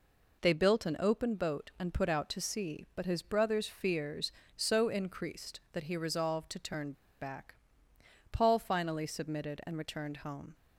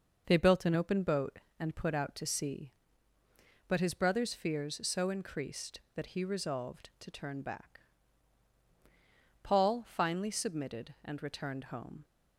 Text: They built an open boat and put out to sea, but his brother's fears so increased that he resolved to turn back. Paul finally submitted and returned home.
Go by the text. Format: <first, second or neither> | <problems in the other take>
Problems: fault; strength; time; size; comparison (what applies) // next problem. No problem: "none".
second | pauses between "turn" and "back"; slight; at 6.9 s; 0.30 s long